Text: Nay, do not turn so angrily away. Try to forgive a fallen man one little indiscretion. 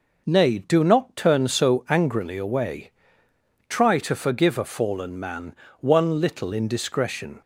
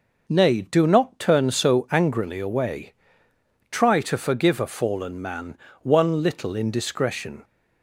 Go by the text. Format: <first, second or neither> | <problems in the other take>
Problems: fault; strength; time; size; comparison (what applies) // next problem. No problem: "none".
neither | pauses between "man" and "one"; slight; the same in both